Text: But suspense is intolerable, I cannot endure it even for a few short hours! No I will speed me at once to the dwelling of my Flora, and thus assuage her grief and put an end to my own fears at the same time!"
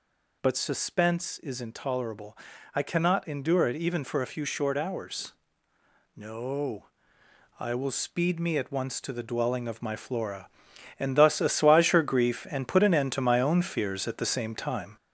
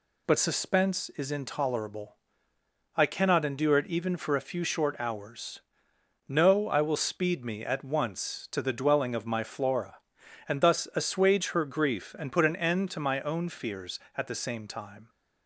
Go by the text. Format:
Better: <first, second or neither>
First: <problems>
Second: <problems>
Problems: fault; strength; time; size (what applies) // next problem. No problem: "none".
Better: second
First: gets louder; noticeable; throughout; 5 dB // pauses between "No" and "I"; noticeable; at 6.8 s; 0.72 s long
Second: none